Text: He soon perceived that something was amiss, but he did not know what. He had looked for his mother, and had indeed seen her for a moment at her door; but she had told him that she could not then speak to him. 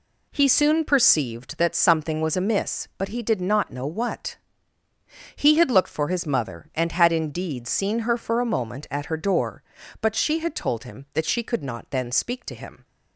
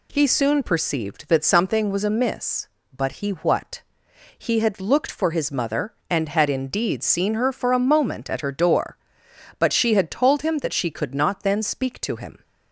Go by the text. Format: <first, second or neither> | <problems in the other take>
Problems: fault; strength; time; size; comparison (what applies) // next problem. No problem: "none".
first | skips "did not know"; at 3.3 s